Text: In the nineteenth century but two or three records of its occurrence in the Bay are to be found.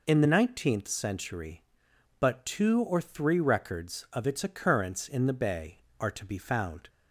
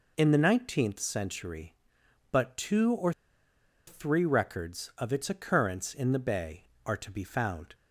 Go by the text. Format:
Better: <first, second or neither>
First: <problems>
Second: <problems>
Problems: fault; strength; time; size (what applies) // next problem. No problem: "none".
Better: first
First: none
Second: pauses between "or" and "three"; noticeable; at 3.1 s; 0.76 s long